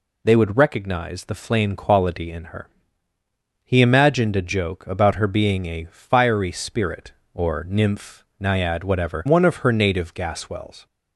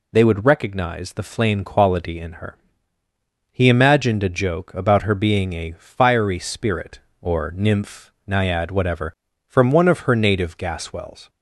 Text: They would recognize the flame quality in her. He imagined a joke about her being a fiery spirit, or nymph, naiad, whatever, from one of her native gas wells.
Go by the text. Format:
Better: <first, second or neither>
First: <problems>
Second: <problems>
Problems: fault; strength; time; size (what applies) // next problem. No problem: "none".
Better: second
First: skips "from"; at 9.2 s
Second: none